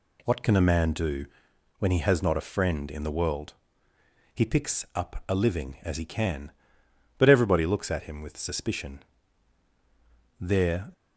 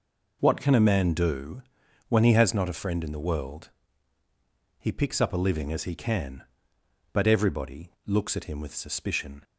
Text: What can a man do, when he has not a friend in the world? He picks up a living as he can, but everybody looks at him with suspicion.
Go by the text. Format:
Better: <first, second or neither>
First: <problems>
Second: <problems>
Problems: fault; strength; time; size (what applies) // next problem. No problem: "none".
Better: second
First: goes on to say "There"; from 10.3 s on; 0.54 s long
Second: none